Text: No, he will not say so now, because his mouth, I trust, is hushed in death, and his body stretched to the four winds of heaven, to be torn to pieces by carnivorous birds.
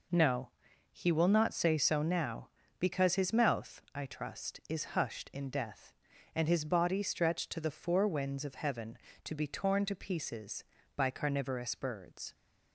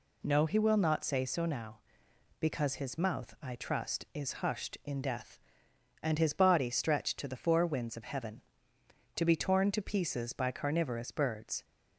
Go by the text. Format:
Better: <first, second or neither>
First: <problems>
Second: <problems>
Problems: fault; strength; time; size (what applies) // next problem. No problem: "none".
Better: neither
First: none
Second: none